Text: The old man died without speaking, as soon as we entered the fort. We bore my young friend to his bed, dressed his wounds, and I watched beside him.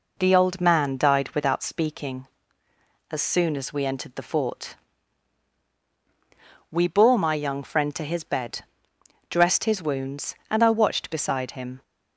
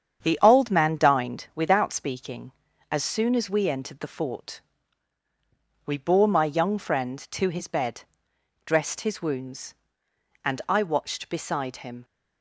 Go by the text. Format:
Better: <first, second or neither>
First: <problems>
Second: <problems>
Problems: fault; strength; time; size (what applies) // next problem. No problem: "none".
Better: first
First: none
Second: starts louder than the rest; strong; until 1.2 s; 8 dB // says "dined" for "died"; at 0.9 s